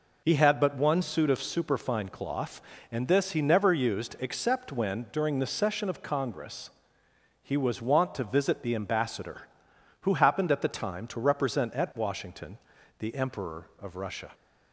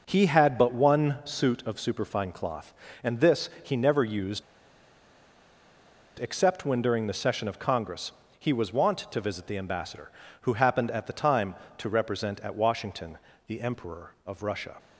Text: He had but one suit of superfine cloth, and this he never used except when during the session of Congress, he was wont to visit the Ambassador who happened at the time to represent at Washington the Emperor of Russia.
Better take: first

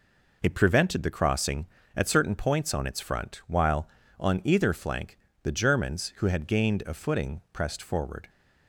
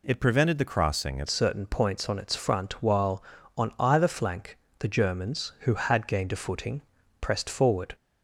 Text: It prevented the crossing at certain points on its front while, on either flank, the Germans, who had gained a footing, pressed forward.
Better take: first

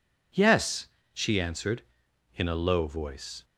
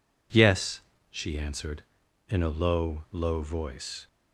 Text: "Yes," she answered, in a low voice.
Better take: first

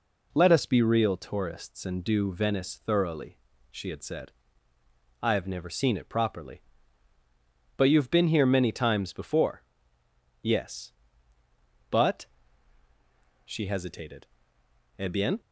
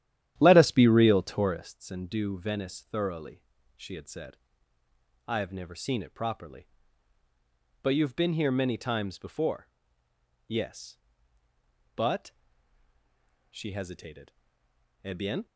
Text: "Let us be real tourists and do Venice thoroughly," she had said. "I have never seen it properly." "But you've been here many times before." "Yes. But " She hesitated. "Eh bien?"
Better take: first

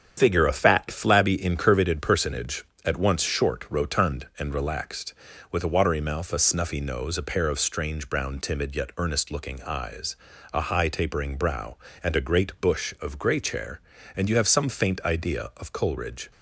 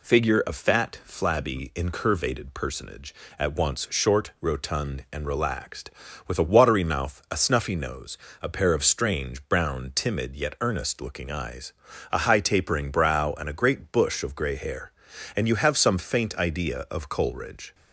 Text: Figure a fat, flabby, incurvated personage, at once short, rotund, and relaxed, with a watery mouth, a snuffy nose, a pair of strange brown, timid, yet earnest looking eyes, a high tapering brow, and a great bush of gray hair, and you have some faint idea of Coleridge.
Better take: second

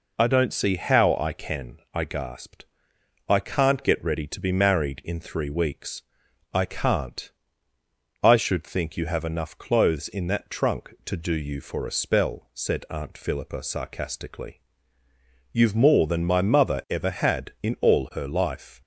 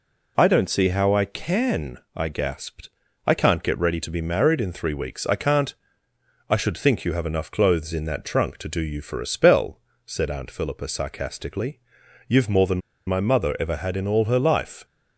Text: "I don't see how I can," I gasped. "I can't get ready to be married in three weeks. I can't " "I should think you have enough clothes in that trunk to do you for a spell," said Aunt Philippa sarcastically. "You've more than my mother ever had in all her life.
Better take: first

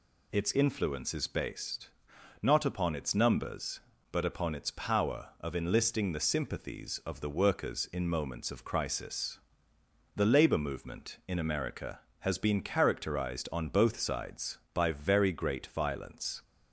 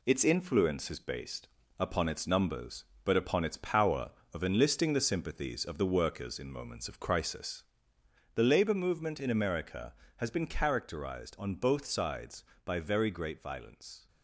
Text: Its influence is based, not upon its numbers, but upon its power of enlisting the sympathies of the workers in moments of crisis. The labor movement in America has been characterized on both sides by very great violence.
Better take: first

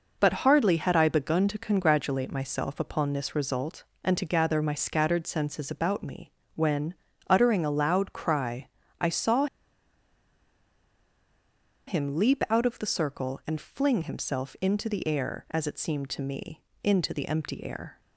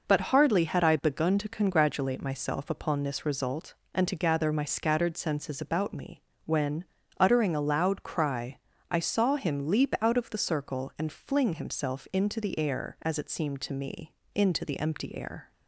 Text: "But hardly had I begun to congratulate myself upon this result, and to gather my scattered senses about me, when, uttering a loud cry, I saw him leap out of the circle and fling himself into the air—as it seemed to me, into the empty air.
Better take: second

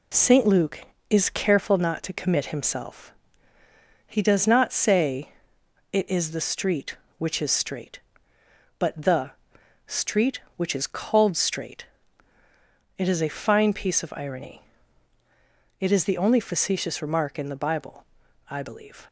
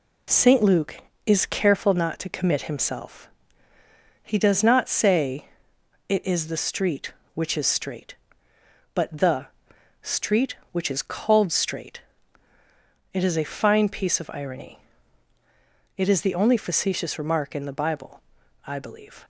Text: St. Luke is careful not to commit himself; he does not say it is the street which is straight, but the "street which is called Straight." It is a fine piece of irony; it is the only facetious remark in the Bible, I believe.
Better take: neither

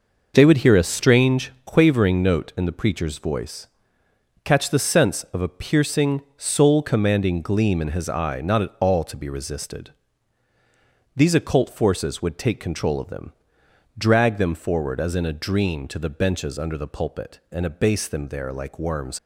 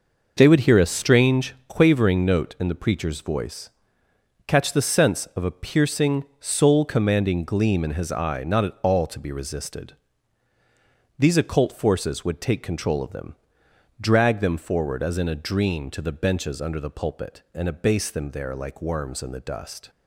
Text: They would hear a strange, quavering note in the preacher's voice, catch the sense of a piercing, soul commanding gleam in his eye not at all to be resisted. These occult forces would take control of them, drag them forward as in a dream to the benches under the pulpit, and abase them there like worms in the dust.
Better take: second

